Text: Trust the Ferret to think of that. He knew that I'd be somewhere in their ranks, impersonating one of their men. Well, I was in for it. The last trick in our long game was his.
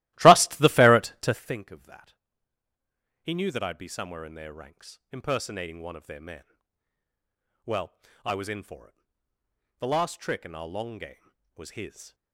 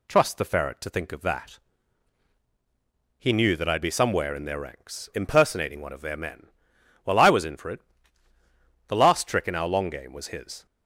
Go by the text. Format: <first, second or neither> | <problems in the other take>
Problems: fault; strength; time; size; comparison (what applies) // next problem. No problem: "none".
second | starts louder than the rest; strong; until 1.6 s; 17 dB